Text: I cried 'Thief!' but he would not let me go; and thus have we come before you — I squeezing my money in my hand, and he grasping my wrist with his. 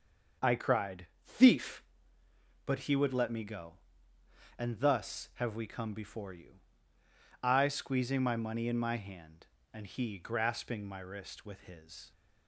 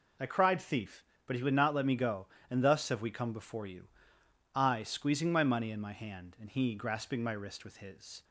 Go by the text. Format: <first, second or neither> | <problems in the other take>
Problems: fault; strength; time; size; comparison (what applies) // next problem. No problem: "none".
second | starts louder than the rest; until 1.6 s; 6.5 dB // pauses between "cried" and "Thief"; slight; at 1.0 s; 0.18 s long // skips "not"; at 3.1 s